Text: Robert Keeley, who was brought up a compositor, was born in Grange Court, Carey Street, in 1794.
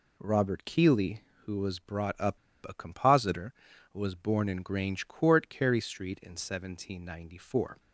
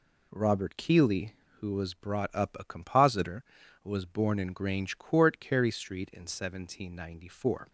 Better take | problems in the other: second | pauses between "up" and "a"; slight; at 2.3 s; 0.29 s long

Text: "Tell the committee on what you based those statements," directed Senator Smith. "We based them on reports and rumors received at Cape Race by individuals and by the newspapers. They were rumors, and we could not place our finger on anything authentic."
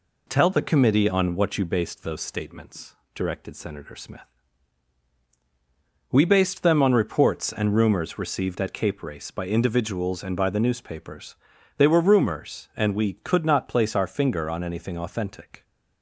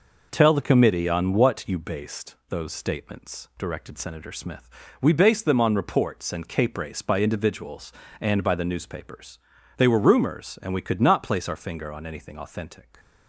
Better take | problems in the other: first | skips "rumors received at"; at 6.4 s

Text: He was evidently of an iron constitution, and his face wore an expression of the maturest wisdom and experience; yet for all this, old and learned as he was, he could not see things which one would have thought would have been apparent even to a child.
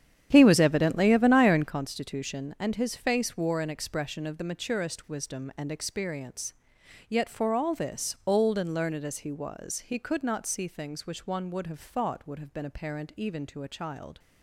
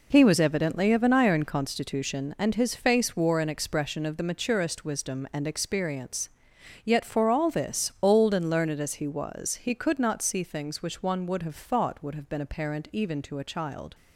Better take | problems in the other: second | starts louder than the rest; strong; until 1.7 s; 9 dB

